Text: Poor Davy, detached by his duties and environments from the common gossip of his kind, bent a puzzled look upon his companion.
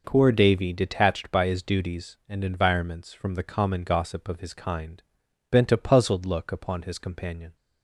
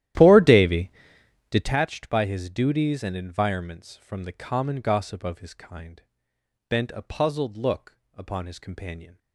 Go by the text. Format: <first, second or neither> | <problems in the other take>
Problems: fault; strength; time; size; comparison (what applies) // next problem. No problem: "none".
first | starts louder than the rest; strong; until 1.7 s; 13 dB // pauses between "look" and "upon"; slight; at 7.9 s; 0.16 s long